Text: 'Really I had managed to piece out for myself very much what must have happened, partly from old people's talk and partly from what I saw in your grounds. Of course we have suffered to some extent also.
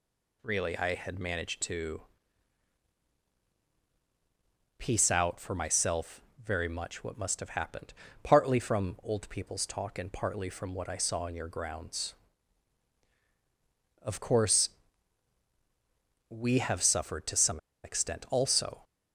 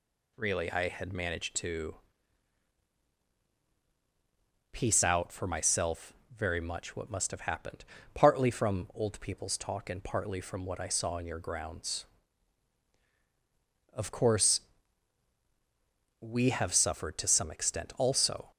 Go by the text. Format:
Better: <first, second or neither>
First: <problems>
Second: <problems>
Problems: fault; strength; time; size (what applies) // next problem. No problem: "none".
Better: second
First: pauses between "to" and "piece"; strong; at 2.0 s; 2.7 s long // pauses between "myself" and "very"; slight; at 6.2 s; 0.20 s long // pauses between "course" and "we"; strong; at 14.6 s; 1.6 s long // pauses between "some" and "extent"; slight; at 17.5 s; 0.24 s long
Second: pauses between "to" and "piece"; strong; at 1.9 s; 2.7 s long // pauses between "myself" and "very"; slight; at 6.1 s; 0.20 s long // pauses between "course" and "we"; strong; at 14.6 s; 1.6 s long